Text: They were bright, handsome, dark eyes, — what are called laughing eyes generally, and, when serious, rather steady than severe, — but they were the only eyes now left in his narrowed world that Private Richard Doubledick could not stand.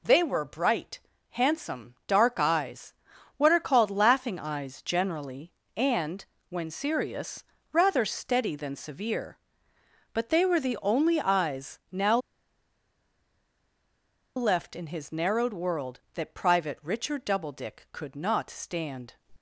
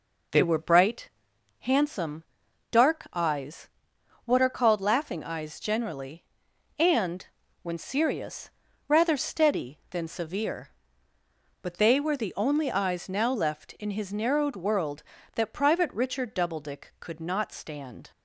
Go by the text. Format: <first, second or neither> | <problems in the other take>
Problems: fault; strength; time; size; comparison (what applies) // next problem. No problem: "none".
second | pauses between "now" and "left"; strong; at 12.1 s; 2.1 s long